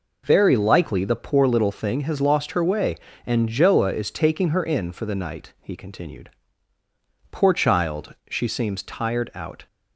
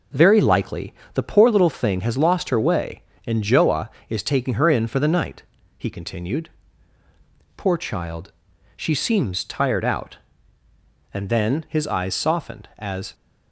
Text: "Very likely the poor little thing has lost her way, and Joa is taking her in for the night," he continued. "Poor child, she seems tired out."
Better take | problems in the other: first | pauses between "likely" and "the"; slight; at 0.9 s; 0.22 s long // goes on to say "And then his eyes softened as"; strong; from 11.1 s on; 2.0 s long

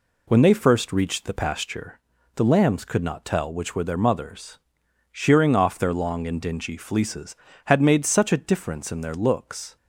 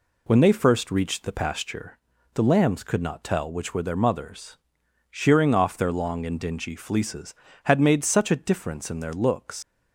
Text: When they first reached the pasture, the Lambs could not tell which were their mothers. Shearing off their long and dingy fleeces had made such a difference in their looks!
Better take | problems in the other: first | leaves "looks" unfinished; at 9.6 s; 125 ms

